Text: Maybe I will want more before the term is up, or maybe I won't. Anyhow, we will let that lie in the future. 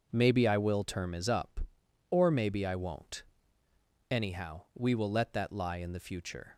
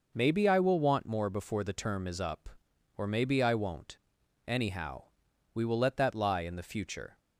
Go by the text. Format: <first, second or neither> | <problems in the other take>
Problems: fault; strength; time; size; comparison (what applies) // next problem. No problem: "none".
second | skips "want more before the"; at 0.8 s